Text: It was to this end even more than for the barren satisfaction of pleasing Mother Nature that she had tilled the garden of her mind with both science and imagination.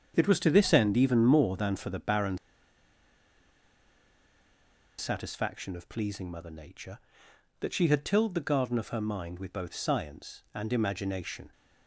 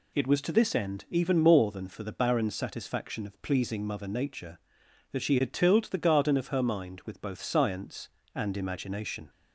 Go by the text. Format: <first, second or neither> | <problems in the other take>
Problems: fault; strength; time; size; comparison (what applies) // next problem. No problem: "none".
second | starts louder than the rest; strong; until 1.1 s; 7.5 dB // pauses between "barren" and "satisfaction"; strong; at 2.3 s; 2.6 s long